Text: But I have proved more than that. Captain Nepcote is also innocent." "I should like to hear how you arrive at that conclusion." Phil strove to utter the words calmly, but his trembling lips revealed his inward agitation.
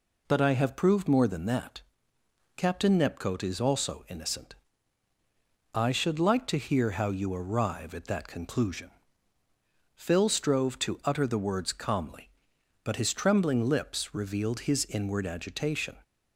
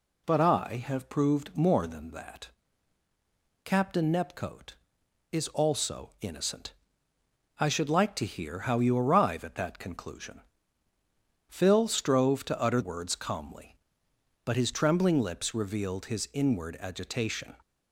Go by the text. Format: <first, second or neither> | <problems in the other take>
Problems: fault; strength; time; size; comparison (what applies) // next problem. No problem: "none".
first | skips "the"; at 12.8 s